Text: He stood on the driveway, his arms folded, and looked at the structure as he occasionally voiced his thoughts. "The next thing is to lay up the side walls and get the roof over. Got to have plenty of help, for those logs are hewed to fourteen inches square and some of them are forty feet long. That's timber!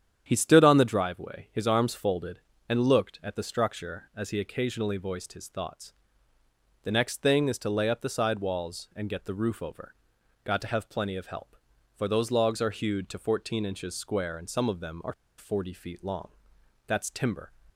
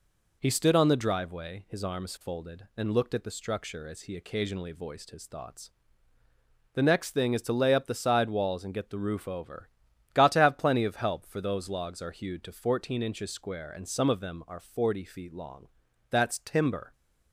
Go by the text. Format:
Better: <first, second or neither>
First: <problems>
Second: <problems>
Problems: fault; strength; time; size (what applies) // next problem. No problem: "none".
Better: second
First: starts louder than the rest; strong; until 1.2 s; 9.5 dB // pauses between "are" and "forty"; slight; at 15.1 s; 0.25 s long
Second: none